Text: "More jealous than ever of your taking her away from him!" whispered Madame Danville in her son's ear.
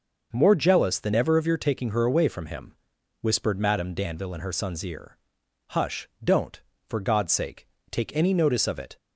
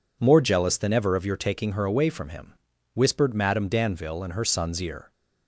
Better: second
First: goes on to say "Hush don't for God's sake take any notice of it"; strong; from 5.7 s on; 3.2 s long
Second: none

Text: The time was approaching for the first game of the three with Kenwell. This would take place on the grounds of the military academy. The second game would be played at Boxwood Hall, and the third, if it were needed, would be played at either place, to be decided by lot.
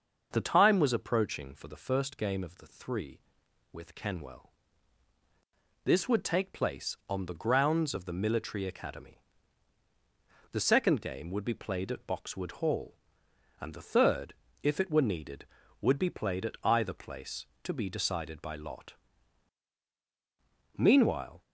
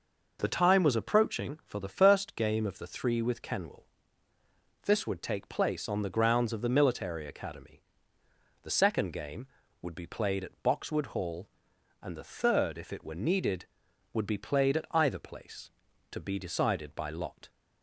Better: second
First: starts louder than the rest; until 1.3 s; 6.5 dB // goes on to say "Meanwhile"; noticeable; from 20.7 s on; 0.64 s long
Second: none

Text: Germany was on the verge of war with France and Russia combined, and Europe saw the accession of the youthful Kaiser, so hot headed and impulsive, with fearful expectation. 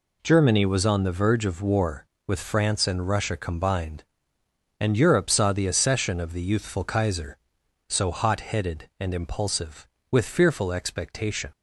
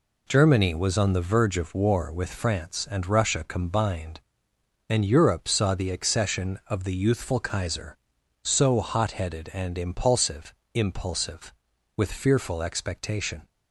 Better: first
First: none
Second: says "impulsive" twice; at 10.7 s

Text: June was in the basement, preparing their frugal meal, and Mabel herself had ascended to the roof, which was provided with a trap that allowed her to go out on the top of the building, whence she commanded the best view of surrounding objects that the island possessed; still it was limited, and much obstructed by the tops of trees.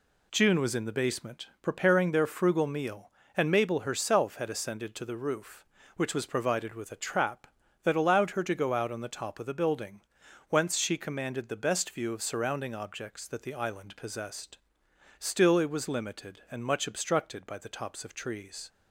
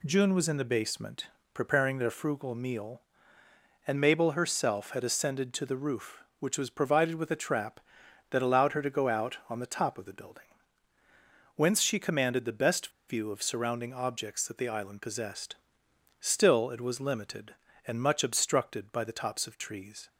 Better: first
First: none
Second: pauses between "best" and "view"; slight; at 12.9 s; 0.16 s long

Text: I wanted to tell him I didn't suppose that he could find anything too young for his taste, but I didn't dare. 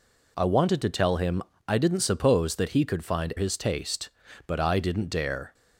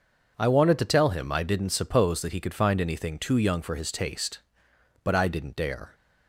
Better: second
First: pauses between "him" and "I"; slight; at 1.4 s; 0.26 s long // skips "anything too young for"; at 3.3 s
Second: none

